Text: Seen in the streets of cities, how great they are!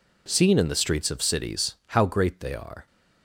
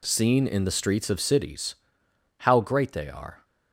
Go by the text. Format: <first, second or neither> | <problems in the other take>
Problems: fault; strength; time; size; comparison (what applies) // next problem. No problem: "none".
neither | none